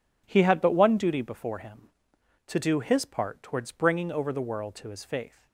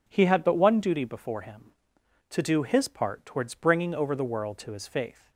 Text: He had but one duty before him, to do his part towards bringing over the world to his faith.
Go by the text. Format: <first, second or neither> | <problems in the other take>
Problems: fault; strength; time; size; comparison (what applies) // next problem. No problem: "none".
second | gets quieter; strong; throughout; 11 dB